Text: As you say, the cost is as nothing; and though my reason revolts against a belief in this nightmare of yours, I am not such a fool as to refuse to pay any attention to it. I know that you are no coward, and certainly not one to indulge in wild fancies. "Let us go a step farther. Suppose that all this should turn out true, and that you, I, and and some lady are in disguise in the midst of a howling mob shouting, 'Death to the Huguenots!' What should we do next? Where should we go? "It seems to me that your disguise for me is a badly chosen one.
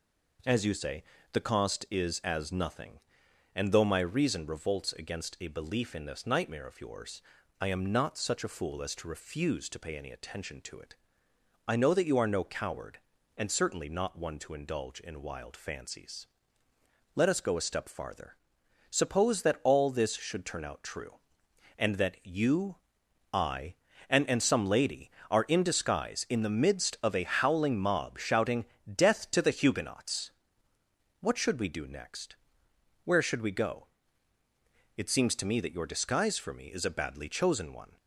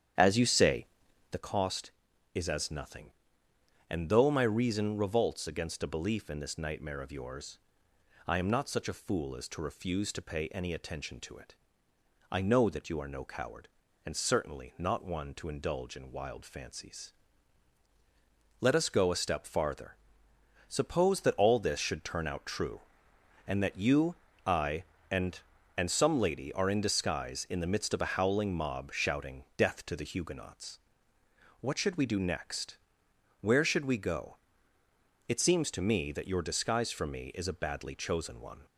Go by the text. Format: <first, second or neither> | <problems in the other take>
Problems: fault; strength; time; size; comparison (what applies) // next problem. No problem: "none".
first | starts louder than the rest; strong; until 1.5 s; 9.5 dB